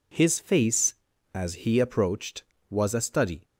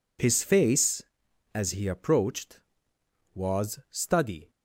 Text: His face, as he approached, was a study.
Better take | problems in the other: first | skips "a"; at 3.8 s

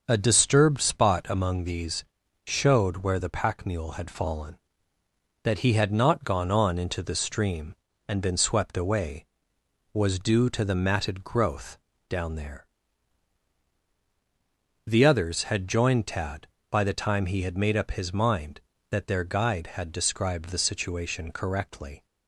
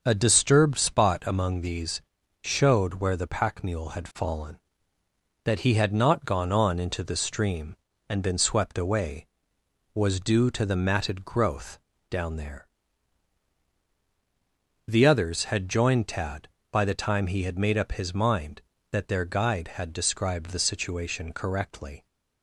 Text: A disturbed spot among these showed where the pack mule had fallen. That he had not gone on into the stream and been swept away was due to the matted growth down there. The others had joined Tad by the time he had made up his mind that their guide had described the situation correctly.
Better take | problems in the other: neither | starts louder than the rest; the same in both // pauses between "these" and "showed"; the same in both // pauses between "growth" and "down"; slight; the same in both

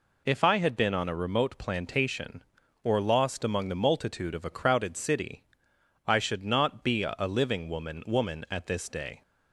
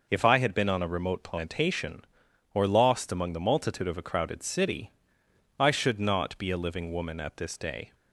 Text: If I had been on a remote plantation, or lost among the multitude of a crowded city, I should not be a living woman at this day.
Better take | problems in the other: second | says "woman" twice; at 8.0 s

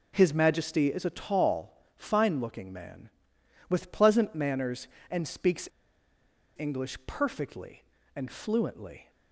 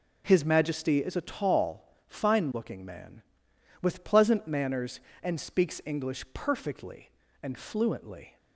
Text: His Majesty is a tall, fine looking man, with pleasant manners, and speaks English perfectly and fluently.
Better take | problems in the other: second | pauses between "speaks" and "English"; noticeable; at 5.6 s; 0.89 s long

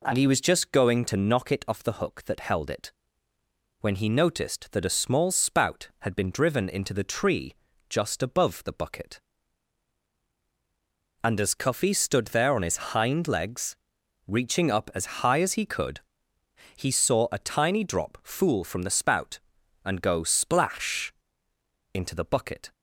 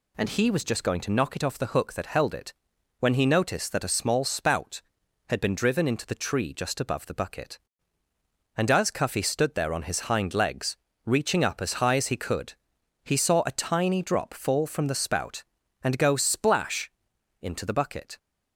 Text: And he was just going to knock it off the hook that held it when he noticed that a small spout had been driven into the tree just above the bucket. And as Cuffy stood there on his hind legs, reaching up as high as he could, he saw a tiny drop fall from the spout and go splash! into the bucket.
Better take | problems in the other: second | pauses between "it" and "when"; noticeable; at 2.9 s; 0.90 s long; noticeable in the second // pauses between "tree" and "just"; slight; at 7.5 s; 0.36 s long // pauses between "his" and "hind"; slight; at 12.7 s; 0.16 s long // says "fool" for "fall"; at 18.2 s

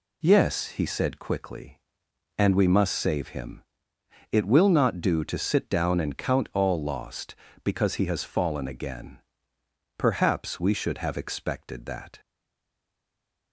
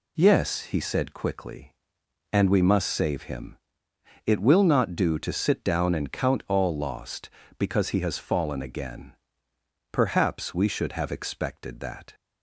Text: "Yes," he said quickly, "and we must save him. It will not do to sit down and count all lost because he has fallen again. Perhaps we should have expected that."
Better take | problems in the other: second | stays silent after the last word; noticeable; from 12.1 s on; 1.4 s long

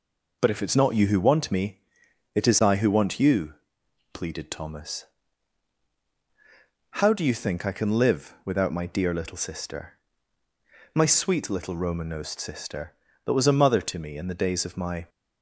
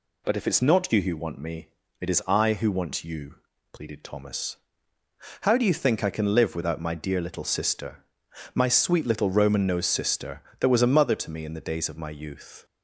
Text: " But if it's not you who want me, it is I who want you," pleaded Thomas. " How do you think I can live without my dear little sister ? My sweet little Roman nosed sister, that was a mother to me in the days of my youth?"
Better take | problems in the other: second | stops before "youth"; at 15.0 s

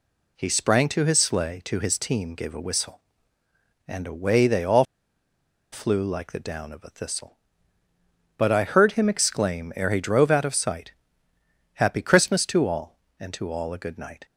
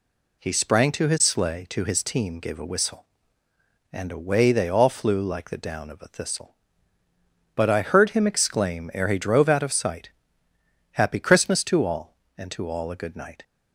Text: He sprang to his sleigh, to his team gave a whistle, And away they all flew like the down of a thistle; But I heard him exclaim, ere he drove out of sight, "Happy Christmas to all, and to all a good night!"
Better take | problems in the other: second | pauses between "all" and "flew"; noticeable; at 4.8 s; 0.88 s long

